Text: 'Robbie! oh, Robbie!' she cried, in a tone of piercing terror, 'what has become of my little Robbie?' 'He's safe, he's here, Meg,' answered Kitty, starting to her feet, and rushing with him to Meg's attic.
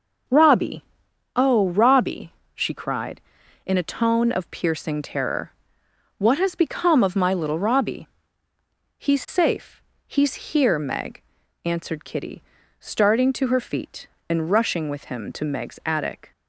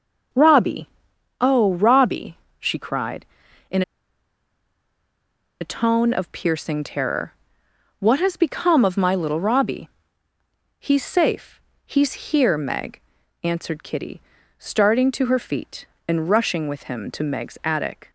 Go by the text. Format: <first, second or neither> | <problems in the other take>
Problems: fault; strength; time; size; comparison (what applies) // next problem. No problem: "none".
first | pauses between "in" and "a"; strong; at 3.8 s; 1.7 s long